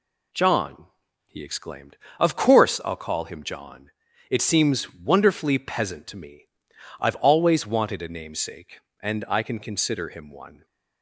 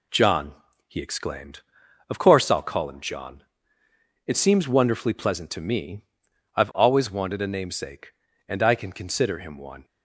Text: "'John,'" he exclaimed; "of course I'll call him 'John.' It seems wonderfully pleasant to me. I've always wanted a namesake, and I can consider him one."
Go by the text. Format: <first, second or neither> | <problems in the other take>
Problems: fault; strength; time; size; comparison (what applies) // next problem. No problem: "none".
second | says "peasant" for "pleasant"; at 5.5 s